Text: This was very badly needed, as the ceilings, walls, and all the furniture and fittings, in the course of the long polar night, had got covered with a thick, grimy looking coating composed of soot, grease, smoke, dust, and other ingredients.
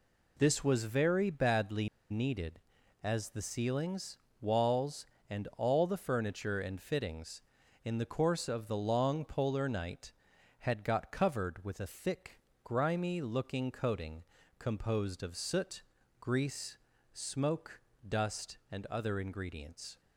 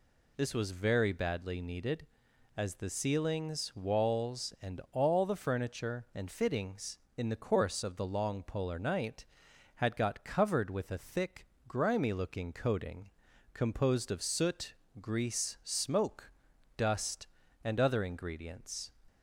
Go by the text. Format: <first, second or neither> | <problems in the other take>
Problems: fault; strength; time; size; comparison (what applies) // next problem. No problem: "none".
second | pauses between "badly" and "needed"; slight; at 1.8 s; 0.23 s long // pauses between "coating" and "composed"; slight; at 14.2 s; 0.34 s long; also in the second